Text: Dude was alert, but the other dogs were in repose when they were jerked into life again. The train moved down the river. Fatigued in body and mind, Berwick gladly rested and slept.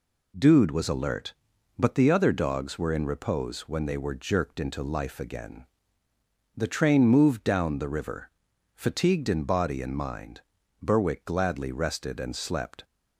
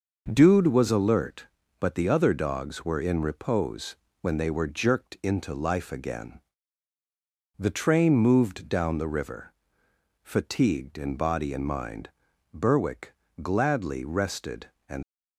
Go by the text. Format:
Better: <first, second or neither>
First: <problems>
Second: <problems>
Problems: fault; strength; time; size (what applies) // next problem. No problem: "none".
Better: first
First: none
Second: pauses between "repose" and "when"; slight; at 3.9 s; 0.28 s long // pauses between "Berwick" and "gladly"; slight; at 13.1 s; 0.30 s long // stops before "slept"; at 15.0 s